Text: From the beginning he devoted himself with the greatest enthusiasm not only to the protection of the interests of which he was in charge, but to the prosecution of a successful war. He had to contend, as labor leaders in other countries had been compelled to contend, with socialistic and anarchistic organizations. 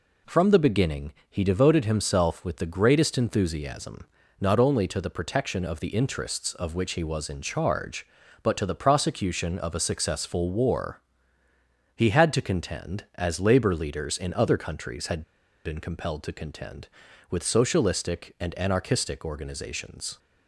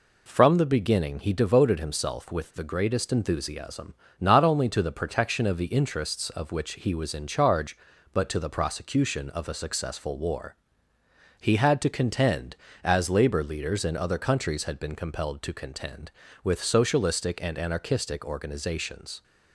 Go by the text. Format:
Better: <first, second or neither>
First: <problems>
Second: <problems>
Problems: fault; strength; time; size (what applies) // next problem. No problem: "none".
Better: second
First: pauses between "beginning" and "he"; slight; at 1.1 s; 0.18 s long // pauses between "enthusiasm" and "not"; slight; at 4.0 s; 0.32 s long // pauses between "had" and "been"; at 15.2 s; 0.43 s long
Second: pauses between "enthusiasm" and "not"; slight; at 3.9 s; 0.26 s long